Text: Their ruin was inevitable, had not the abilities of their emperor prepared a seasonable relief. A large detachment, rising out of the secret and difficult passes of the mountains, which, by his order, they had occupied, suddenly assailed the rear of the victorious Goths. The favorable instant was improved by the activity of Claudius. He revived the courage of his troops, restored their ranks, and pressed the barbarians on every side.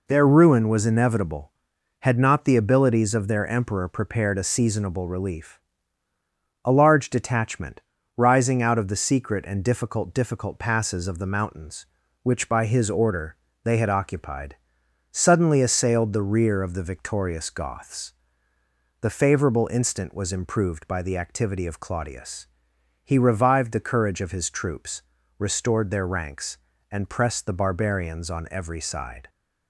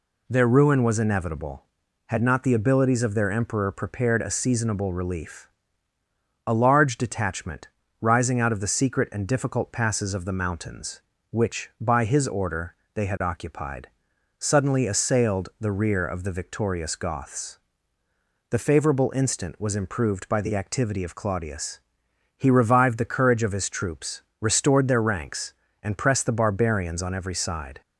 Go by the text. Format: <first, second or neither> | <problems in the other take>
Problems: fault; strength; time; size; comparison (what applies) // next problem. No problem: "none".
second | says "difficult" twice; at 10.1 s